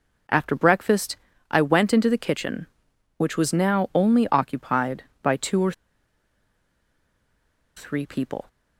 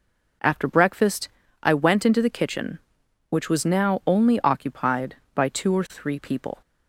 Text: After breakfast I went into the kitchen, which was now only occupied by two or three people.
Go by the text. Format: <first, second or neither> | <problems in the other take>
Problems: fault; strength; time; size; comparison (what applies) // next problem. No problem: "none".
second | pauses between "breakfast" and "I"; slight; at 1.1 s; 0.34 s long; slight in the second // pauses between "or" and "three"; strong; at 5.7 s; 2.0 s long